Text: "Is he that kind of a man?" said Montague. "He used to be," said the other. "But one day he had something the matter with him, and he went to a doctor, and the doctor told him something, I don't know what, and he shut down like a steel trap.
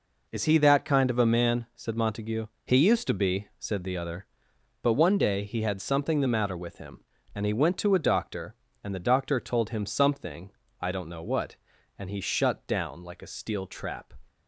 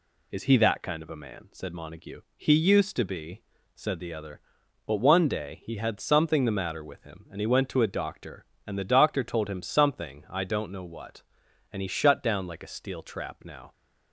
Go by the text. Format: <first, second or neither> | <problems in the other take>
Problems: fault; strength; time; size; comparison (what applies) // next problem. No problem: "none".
first | goes on to say "Now"; slight; from 13.4 s on; 0.28 s long